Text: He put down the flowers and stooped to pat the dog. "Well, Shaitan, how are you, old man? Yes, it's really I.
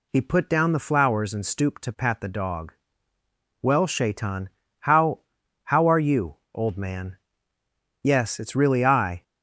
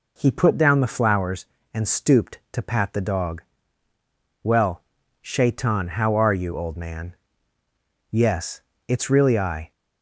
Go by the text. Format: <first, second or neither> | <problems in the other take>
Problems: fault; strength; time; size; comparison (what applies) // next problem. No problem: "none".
second | says "how" twice; at 5.6 s